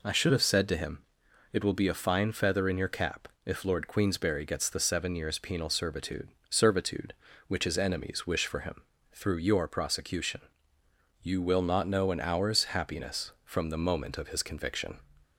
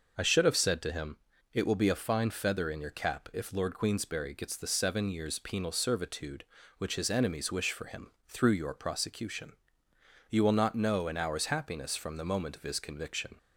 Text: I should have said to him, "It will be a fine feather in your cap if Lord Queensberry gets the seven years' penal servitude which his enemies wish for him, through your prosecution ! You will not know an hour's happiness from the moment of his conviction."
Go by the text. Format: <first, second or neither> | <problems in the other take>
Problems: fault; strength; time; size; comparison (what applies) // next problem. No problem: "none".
second | pauses between "cap" and "if"; slight; at 3.2 s; 0.16 s long // says "servitude" twice; at 6.4 s